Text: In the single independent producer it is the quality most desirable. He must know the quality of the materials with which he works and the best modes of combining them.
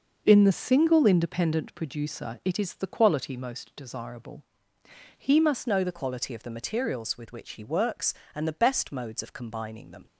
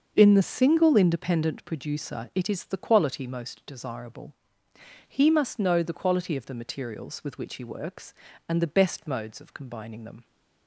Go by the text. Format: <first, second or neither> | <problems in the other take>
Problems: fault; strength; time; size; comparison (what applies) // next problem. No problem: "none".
second | starts louder than the rest; noticeable; until 1.2 s; 6 dB; also in the second // changes voice at "know"; from 5.6 s on; 4.4 s long